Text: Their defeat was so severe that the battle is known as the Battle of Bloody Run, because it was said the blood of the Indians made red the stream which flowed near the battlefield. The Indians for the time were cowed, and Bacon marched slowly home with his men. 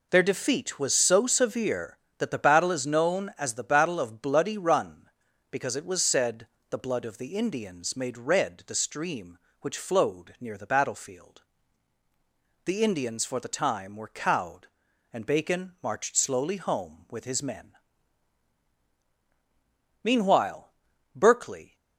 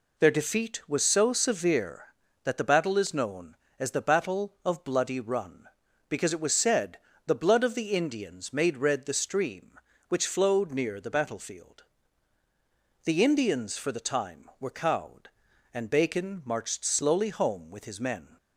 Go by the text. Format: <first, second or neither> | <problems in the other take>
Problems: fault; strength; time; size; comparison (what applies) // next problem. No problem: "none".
second | pauses between "said" and "the"; slight; at 6.4 s; 0.24 s long; slight in the second // goes on to say "Meanwhile Berkeley"; strong; from 20.0 s on; 1.7 s long